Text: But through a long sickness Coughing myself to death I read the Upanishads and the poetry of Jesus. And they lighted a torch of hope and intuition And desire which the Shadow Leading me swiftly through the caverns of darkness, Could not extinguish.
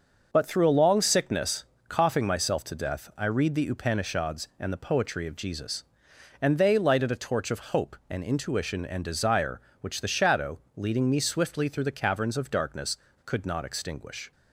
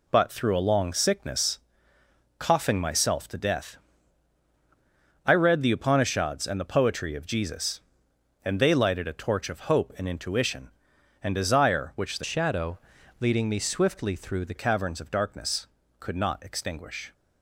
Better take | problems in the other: first | pauses between "sickness" and "Coughing"; noticeable; at 1.5 s; 0.80 s long; slight in the first // pauses between "death" and "I"; strong; at 3.7 s; 1.4 s long // changes voice from "Shadow" to "the"; from 12.2 to 14.5 s; 2.3 s long // pauses between "Shadow" and "Leading"; at 12.7 s; 0.42 s long; slight in the first

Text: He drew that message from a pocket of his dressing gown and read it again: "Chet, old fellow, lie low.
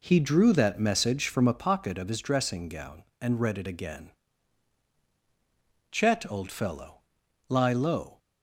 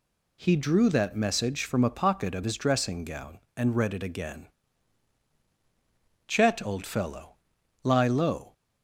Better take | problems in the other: second | starts louder than the rest; until 1.6 s; 3.5 dB

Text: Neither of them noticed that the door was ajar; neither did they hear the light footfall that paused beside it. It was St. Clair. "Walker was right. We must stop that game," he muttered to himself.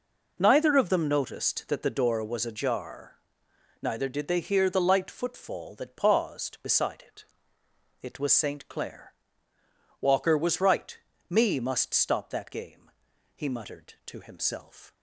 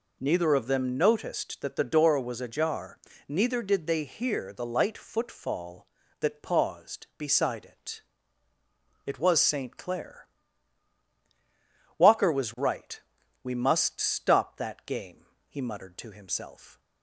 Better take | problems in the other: second | says "Me" for "We"; at 11.2 s

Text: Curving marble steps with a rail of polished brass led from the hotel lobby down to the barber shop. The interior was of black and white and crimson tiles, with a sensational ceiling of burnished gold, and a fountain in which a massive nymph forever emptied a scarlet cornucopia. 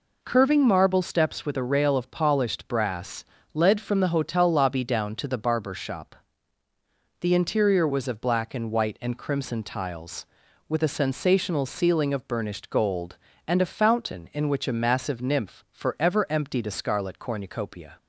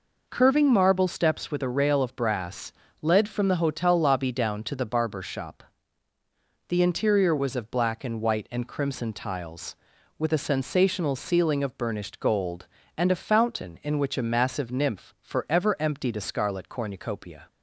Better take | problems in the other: first | skips "polished"; at 2.1 s // pauses between "brass" and "led"; slight; at 2.7 s; 0.30 s long; slight in the first

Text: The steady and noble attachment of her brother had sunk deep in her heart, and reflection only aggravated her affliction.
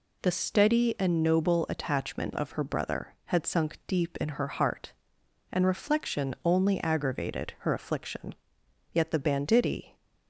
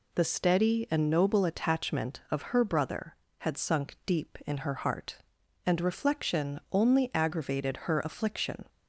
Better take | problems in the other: second | goes on to say "Yet the banditti"; noticeable; from 8.9 s on; 1.0 s long

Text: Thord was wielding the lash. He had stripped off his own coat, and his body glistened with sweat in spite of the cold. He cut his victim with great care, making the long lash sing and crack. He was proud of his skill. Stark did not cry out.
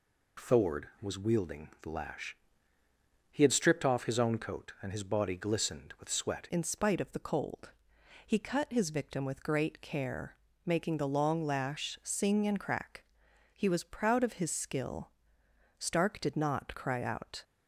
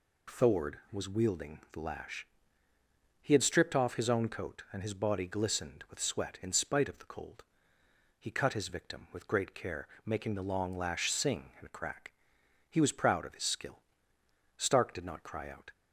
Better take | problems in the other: second | changes voice at "in"; from 6.4 s on; 11.0 s long

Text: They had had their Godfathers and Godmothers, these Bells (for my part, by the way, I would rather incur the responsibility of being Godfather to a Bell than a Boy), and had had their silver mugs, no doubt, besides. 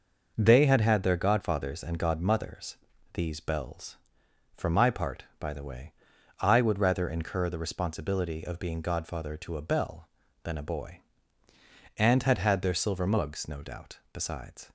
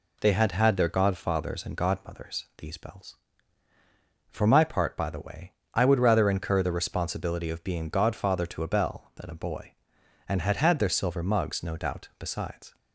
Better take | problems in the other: neither | none

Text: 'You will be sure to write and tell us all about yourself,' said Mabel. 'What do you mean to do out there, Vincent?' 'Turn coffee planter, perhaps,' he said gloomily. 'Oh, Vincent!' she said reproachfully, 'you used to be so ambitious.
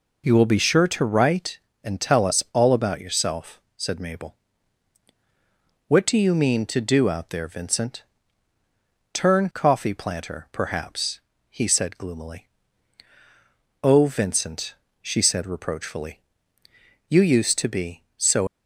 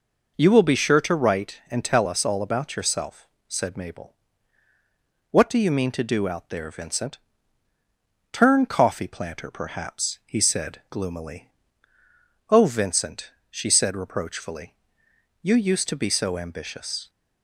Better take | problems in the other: second | stops before "ambitious"; at 18.4 s

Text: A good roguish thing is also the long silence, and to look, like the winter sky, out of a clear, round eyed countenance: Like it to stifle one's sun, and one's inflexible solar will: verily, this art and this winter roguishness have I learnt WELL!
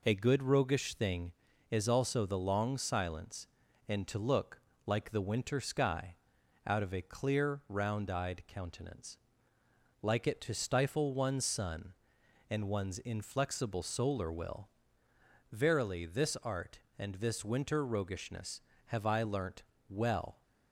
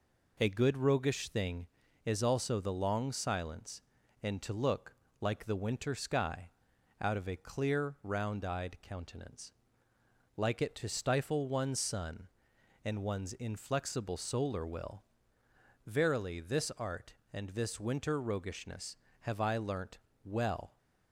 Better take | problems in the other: neither | pauses between "learnt" and "WELL"; slight; the same in both

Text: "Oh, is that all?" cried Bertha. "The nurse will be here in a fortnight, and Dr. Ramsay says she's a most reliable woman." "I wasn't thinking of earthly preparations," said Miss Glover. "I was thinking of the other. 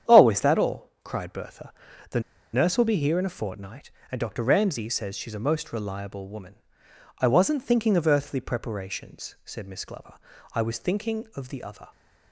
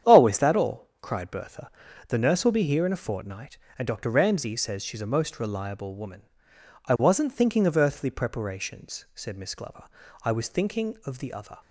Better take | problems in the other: second | starts louder than the rest; strong; until 1.1 s; 9 dB; strong in the second // pauses between "The" and "nurse"; slight; at 2.1 s; 0.33 s long

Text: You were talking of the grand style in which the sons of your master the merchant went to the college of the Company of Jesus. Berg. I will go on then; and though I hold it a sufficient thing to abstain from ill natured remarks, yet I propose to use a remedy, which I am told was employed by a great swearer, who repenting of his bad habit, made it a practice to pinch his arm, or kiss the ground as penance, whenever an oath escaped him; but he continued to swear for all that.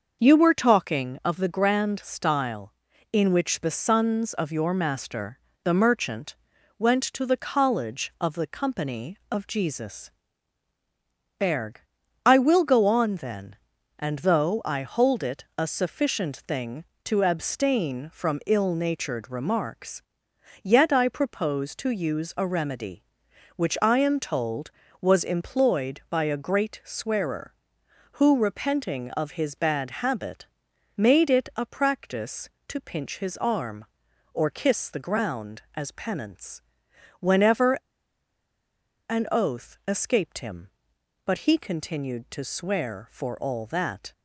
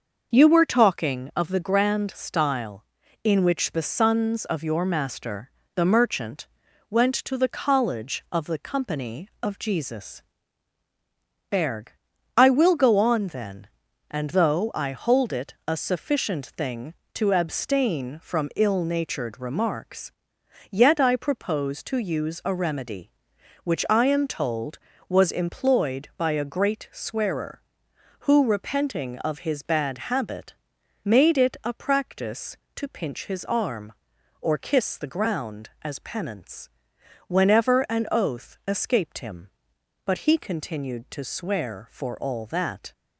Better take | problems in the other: second | starts louder than the rest; until 1.2 s; 6 dB; noticeable in the second // pauses between "master" and "the"; slight; at 5.3 s; 0.26 s long; slight in the second // pauses between "merchant" and "went"; at 6.3 s; 0.42 s long; also in the second // pauses between "whenever" and "an"; strong; at 37.7 s; 1.3 s long

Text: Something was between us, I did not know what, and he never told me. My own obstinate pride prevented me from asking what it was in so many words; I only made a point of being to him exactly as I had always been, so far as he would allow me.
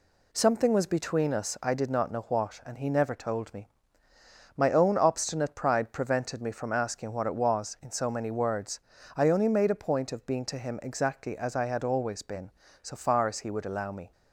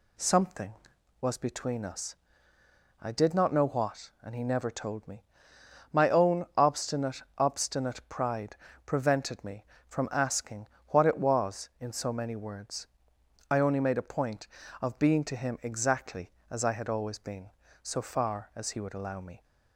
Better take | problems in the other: first | says "obstinate" twice; at 7.3 s // pauses between "pride" and "prevented"; slight; at 8.5 s; 0.28 s long // pauses between "asking" and "what"; slight; at 10.6 s; 0.22 s long

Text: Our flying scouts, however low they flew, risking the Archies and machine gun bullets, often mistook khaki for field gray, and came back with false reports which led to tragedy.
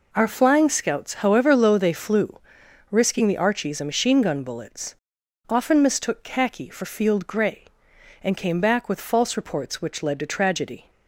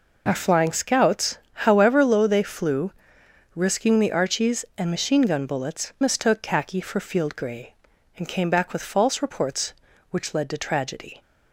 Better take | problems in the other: first | skips "often"; at 5.9 s

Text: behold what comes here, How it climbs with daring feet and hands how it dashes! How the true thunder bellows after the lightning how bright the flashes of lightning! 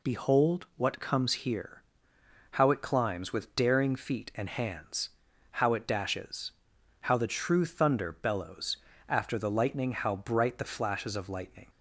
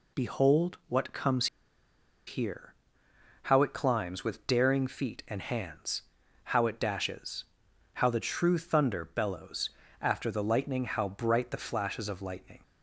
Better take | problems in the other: first | pauses between "comes" and "here"; noticeable; at 1.4 s; 0.81 s long // pauses between "hands" and "how"; at 6.0 s; 0.42 s long; also in the first // pauses between "bellows" and "after"; slight; at 9.6 s; 0.32 s long; slight in the first

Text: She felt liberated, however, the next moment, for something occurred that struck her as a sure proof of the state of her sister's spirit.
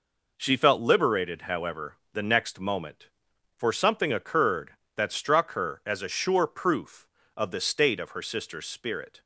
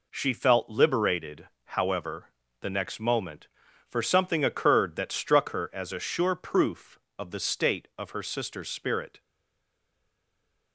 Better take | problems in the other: first | stays silent after the last word; noticeable; from 9.1 s on; 1.6 s long

